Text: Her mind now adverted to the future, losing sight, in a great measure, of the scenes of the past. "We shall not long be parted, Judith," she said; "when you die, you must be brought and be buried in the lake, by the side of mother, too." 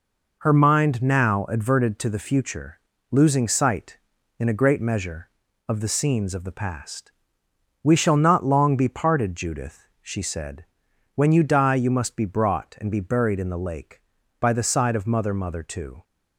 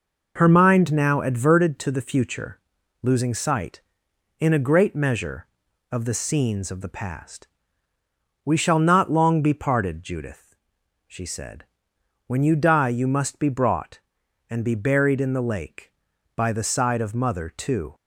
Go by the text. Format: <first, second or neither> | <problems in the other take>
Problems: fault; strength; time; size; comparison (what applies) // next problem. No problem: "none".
second | says "mother" twice; at 15.3 s